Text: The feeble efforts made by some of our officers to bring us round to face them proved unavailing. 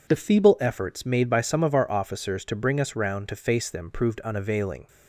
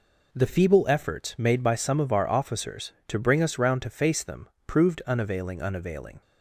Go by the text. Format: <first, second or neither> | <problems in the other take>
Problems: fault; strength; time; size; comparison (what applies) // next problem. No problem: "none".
first | pauses between "them" and "proved"; slight; at 4.4 s; 0.18 s long // says "unavailing" twice; at 5.6 s